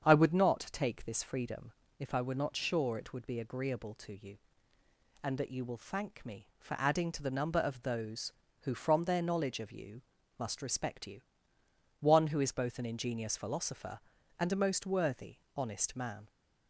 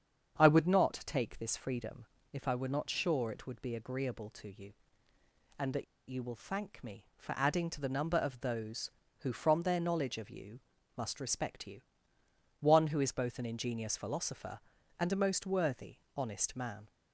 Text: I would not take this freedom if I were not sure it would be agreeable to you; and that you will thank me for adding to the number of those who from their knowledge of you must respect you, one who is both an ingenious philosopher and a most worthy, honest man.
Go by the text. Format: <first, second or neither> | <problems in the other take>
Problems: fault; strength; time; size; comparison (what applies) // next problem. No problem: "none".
first | starts louder than the rest; strong; until 1.4 s; 7.5 dB; strong in the first // pauses between "freedom" and "if"; slight; at 2.0 s; 0.26 s long; slight in the first // pauses between "that" and "you"; slight; at 5.8 s; 0.24 s long // pauses between "you" and "must"; at 10.5 s; 0.38 s long; also in the first